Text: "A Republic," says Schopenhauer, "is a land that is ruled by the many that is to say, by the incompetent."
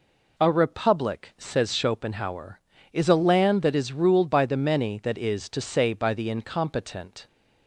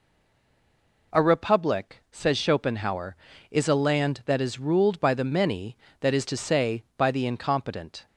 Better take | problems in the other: first | stays silent before the first word; until 1.1 s; 1.1 s long

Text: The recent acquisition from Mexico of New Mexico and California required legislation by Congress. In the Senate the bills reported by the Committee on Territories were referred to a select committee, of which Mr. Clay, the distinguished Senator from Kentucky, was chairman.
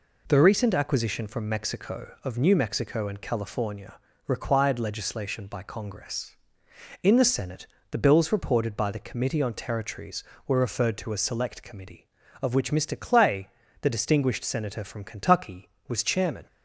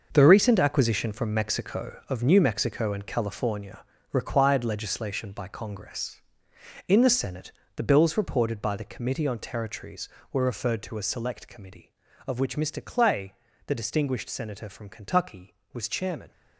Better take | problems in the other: first | gets quieter; strong; throughout; 10.5 dB // pauses between "California" and "required"; slight; at 3.8 s; 0.26 s long; slight in the first // pauses between "Senate" and "the"; slight; at 7.5 s; 0.24 s long; slight in the first

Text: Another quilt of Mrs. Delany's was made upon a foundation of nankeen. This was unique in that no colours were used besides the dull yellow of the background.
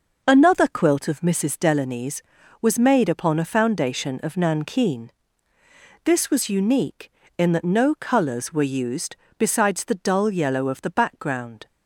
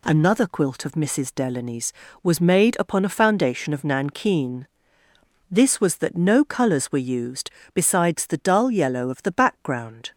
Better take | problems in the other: first | skips "unique in"; at 5.9 s // pauses between "used" and "besides"; slight; at 7.4 s; 0.24 s long; slight in the first

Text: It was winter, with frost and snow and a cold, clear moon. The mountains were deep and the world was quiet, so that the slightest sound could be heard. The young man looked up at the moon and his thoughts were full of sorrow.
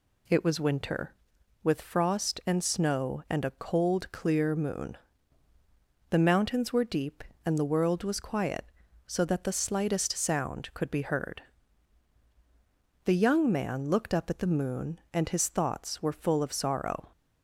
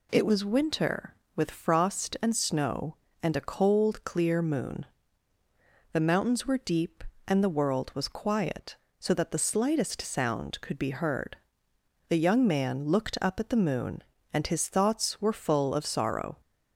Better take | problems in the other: neither | none

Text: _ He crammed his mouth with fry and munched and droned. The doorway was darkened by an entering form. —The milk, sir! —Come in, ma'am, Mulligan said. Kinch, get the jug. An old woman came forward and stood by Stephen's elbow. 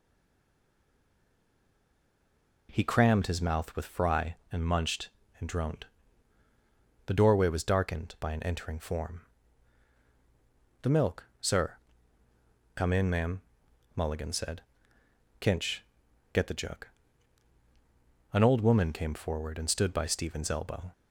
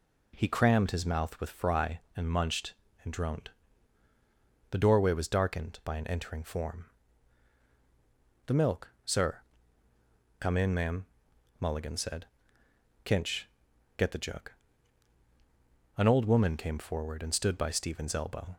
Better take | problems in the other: second | stays silent before the first word; strong; until 2.6 s; 2.6 s long

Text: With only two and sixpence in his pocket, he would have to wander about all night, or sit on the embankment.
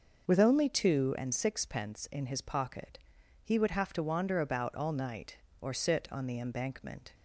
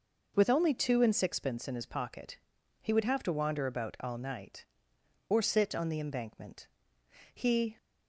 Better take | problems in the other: first | goes on to say "He"; slight; from 7.3 s on; 0.44 s long

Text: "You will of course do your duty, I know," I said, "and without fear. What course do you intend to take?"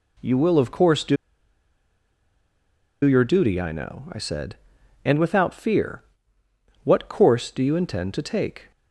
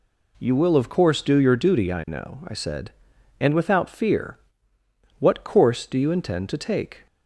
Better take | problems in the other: second | pauses between "do" and "your"; strong; at 1.1 s; 1.8 s long

